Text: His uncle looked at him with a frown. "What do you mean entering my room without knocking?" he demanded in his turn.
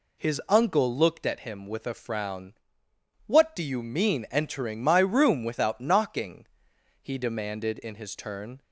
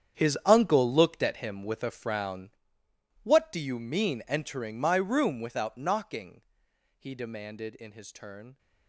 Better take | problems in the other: first | gets quieter; strong; throughout; 15.5 dB

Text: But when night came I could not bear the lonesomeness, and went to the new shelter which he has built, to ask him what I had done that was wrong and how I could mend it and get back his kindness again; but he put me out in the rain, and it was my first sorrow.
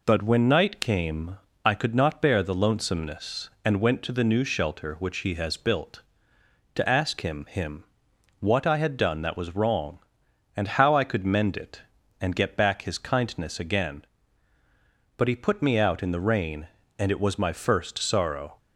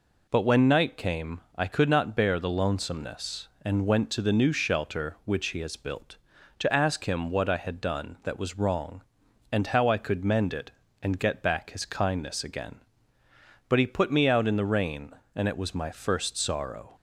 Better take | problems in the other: second | pauses between "came" and "I"; slight; at 1.3 s; 0.28 s long; slight in the second // says "him" twice; at 7.4 s

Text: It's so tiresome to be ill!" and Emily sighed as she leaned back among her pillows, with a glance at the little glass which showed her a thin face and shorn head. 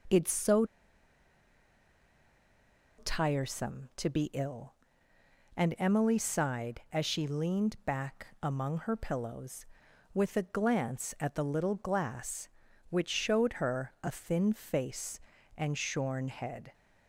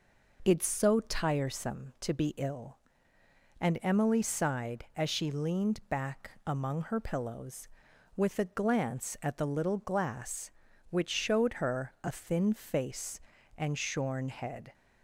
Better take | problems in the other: second | pauses between "so" and "tiresome"; strong; at 0.6 s; 2.3 s long // pauses between "back" and "among"; slight; at 8.2 s; 0.16 s long; slight in the second

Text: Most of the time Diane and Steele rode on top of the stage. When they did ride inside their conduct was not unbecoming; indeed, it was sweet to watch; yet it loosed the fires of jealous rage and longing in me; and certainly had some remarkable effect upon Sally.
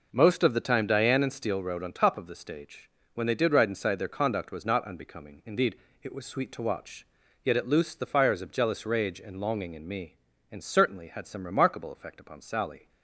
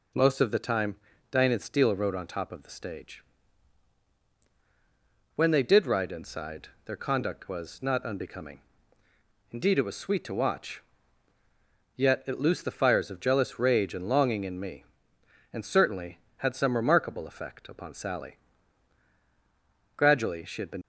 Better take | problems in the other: first | pauses between "time" and "Diane"; slight; at 0.9 s; 0.34 s long // pauses between "inside" and "their"; slight; at 6.6 s; 0.16 s long // goes on to say "Gradually she had been"; noticeable; from 19.9 s on; 0.84 s long

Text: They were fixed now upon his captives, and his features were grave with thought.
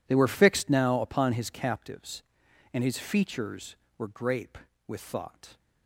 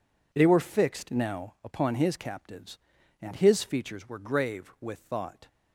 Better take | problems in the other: second | says "grape" for "grave"; at 4.0 s

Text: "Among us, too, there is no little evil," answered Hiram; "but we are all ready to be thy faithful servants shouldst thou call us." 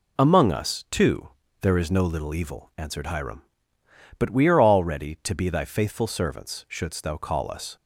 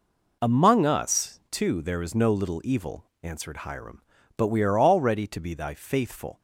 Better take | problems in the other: first | stops before "servants shouldst thou call us"; at 6.3 s

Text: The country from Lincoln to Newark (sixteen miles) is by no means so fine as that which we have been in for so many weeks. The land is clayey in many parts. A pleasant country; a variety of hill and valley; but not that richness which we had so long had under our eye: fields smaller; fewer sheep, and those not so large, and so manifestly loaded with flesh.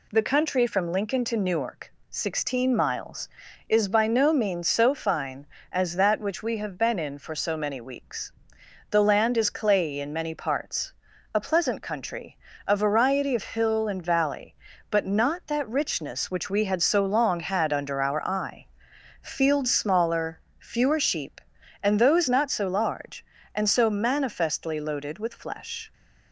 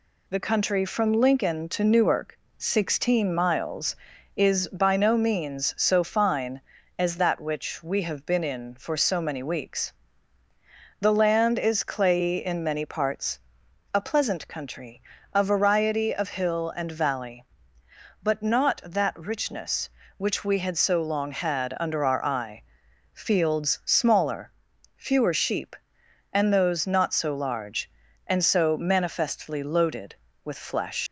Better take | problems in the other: first | leaves "flesh" unfinished; at 31.0 s; 105 ms

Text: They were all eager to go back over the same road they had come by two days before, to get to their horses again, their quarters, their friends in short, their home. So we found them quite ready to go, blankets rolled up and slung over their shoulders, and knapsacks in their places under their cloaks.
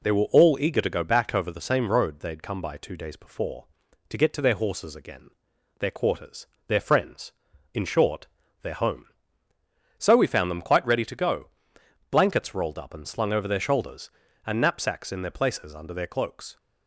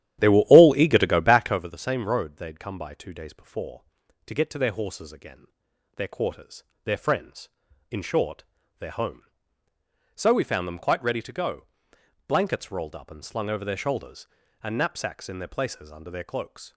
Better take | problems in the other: first | starts louder than the rest; strong; until 1.7 s; 11 dB

